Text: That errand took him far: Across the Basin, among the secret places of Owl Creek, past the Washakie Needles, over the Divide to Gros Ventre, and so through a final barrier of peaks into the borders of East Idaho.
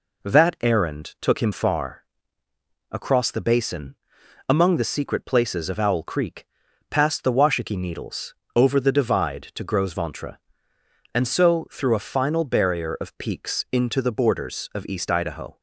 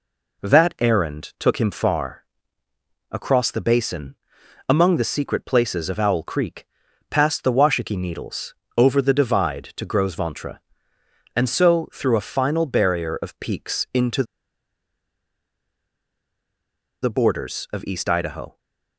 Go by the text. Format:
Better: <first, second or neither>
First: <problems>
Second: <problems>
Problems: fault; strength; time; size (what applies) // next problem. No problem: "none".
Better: first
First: none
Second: pauses between "into" and "the"; strong; at 14.2 s; 2.7 s long